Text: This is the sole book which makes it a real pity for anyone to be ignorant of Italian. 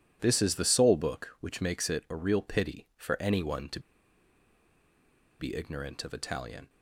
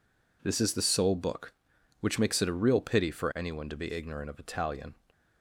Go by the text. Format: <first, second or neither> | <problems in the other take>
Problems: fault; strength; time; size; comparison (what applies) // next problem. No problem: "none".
second | pauses between "to" and "be"; strong; at 3.7 s; 1.5 s long